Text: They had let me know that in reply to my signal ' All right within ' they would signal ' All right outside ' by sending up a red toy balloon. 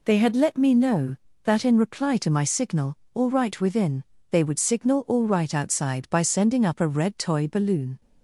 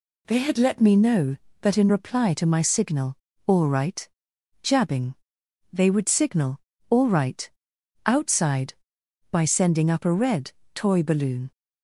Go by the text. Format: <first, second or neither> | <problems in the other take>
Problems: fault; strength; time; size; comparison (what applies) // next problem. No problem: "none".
first | says "jabbing" for "within"; at 4.6 s // pauses between "right" and "outside"; noticeable; at 7.4 s; 0.60 s long // pauses between "red" and "toy"; slight; at 10.5 s; 0.22 s long